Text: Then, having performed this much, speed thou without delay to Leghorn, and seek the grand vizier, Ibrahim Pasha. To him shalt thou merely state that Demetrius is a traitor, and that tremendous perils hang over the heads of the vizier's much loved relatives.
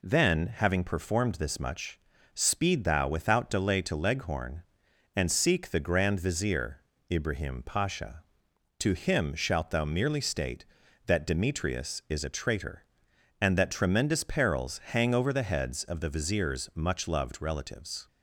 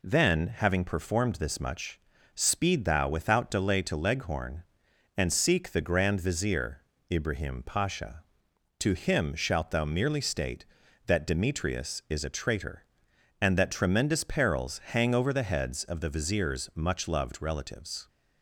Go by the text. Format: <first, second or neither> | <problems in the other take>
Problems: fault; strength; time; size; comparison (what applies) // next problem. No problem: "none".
neither | none